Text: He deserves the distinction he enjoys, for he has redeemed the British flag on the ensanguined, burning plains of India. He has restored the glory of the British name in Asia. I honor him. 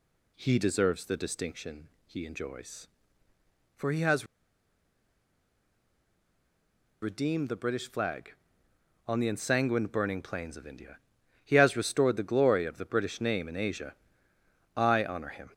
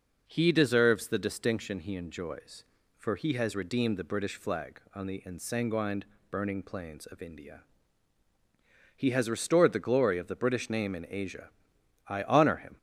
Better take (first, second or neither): second